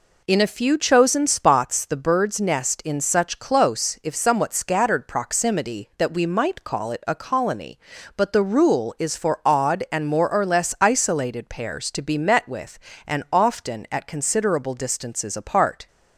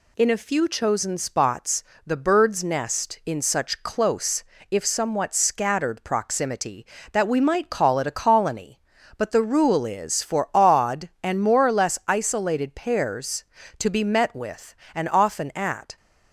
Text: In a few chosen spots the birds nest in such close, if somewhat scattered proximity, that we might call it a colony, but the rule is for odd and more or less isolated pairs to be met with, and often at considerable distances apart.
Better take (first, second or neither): first